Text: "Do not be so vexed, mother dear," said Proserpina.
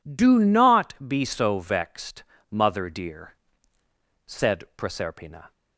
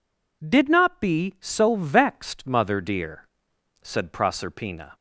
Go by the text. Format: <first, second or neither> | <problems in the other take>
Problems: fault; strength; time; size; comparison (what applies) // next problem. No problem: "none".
first | says "Did" for "Do"; at 0.4 s